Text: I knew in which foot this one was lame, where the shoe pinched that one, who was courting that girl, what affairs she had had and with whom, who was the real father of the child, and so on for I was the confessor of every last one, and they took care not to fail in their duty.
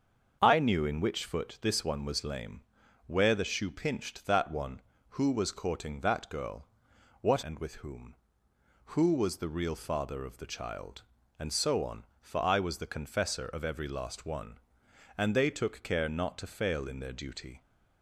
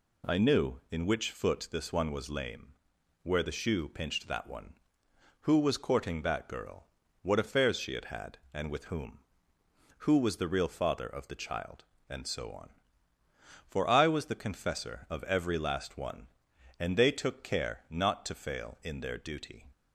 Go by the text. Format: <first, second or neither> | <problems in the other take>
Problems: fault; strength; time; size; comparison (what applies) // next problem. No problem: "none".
second | starts louder than the rest; until 1.4 s; 7 dB // skips "affairs she had had"; at 7.4 s